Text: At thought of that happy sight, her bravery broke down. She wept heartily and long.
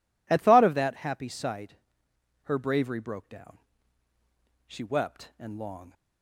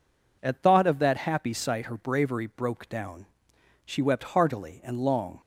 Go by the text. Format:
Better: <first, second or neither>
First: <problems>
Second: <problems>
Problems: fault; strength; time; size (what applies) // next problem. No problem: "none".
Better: second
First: skips "heartily"; at 5.3 s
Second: none